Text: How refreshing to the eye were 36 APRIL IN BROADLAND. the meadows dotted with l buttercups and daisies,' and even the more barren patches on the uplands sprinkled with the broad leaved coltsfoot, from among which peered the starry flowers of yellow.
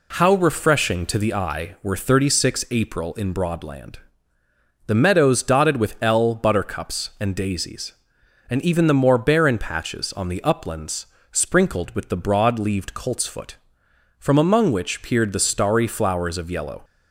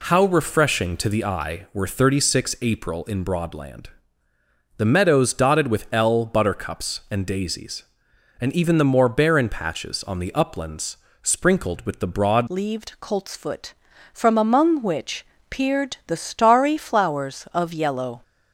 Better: first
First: pauses between "uplands" and "sprinkled"; slight; at 11.0 s; 0.26 s long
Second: pauses between "uplands" and "sprinkled"; slight; at 10.9 s; 0.26 s long // changes voice at "leaved"; from 12.4 s on; 5.8 s long // pauses between "which" and "peered"; slight; at 15.2 s; 0.24 s long

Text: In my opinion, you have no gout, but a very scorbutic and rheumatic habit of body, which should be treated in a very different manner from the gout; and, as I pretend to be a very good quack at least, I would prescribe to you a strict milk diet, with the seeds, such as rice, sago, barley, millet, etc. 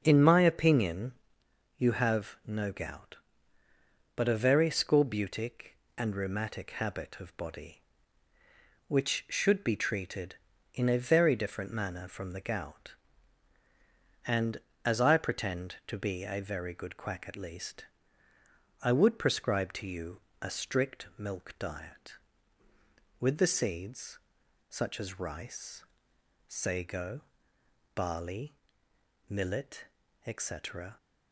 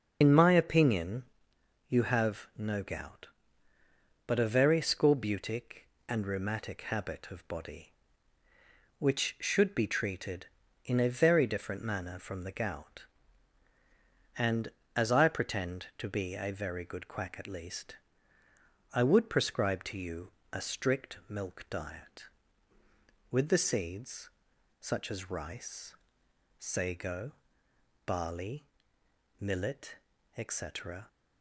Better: first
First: starts louder than the rest; until 1.0 s; 6.5 dB // pauses between "you" and "a"; slight; at 20.1 s; 0.22 s long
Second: loses the start of "In"; at 0.2 s; 70 ms // starts louder than the rest; until 1.2 s; 6 dB // pauses between "you" and "a"; slight; at 20.2 s; 0.22 s long

